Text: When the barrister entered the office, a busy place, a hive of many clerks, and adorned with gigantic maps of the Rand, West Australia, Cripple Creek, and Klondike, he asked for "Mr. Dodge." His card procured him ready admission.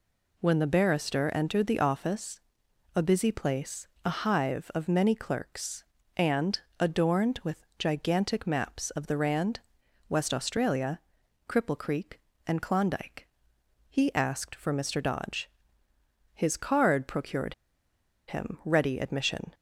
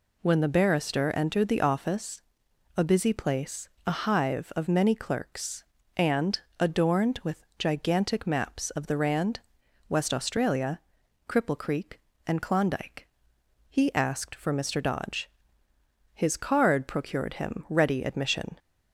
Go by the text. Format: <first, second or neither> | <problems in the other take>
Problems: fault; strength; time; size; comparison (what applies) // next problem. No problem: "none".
second | pauses between "and" and "adorned"; slight; at 6.5 s; 0.20 s long; slight in the second // pauses between "procured" and "him"; noticeable; at 17.5 s; 0.74 s long